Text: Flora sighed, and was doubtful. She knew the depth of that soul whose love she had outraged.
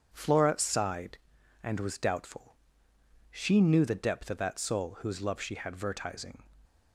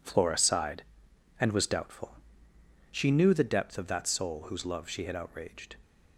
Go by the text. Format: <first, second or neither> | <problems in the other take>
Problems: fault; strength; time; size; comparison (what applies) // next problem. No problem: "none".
second | starts louder than the rest; strong; until 1.1 s; 7.5 dB // says "vertising" for "outraged"; at 5.7 s